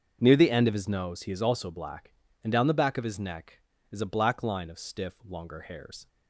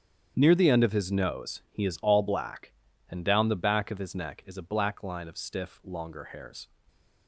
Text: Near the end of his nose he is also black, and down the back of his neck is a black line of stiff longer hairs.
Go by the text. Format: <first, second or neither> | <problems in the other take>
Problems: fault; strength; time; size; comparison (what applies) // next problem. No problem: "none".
first | starts louder than the rest; strong; until 1.3 s; 8.5 dB; also in the first // says "all" for "also"; at 2.0 s